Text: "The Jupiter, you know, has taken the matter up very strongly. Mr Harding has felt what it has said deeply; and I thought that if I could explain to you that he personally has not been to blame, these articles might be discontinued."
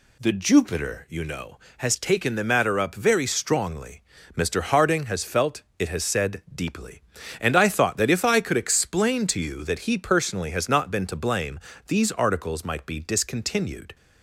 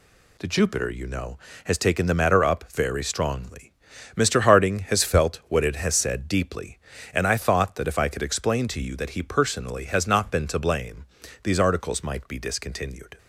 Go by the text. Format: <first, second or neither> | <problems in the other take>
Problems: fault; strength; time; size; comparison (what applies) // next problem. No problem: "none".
second | skips "what"; at 5.7 s